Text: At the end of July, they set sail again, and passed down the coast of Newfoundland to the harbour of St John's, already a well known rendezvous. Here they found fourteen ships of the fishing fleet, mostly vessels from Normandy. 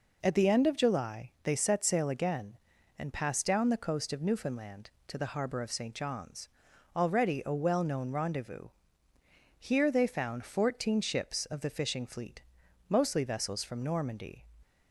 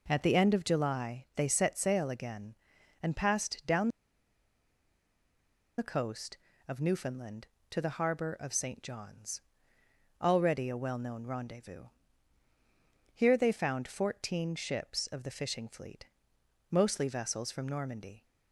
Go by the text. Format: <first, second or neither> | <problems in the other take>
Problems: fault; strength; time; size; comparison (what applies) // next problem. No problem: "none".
first | pauses between "down" and "the"; strong; at 3.8 s; 1.8 s long